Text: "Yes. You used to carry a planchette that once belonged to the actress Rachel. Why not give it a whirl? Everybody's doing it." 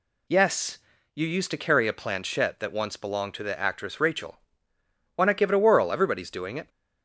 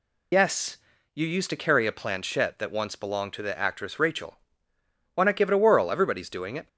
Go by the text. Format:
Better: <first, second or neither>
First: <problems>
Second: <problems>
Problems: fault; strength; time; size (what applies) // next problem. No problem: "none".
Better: first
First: none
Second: loses the start of "Yes"; at 0.3 s; 40 ms